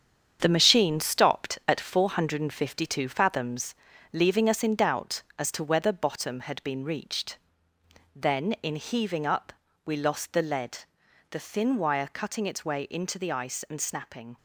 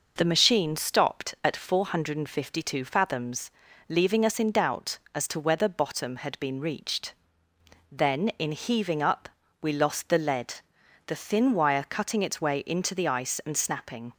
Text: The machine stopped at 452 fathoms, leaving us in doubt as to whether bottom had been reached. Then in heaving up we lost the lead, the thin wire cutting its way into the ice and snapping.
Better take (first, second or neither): second